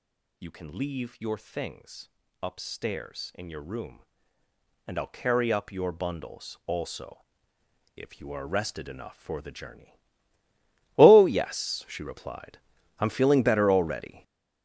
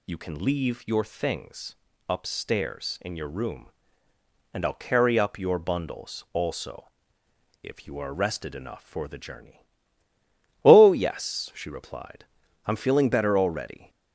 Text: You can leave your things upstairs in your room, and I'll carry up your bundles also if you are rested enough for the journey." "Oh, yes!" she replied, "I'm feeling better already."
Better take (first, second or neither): second